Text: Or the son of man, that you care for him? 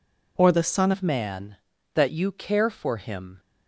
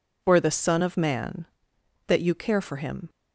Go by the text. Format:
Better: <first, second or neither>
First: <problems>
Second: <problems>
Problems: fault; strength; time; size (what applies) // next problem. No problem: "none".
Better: second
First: changes voice at "of"; from 0.9 s on; 2.4 s long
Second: none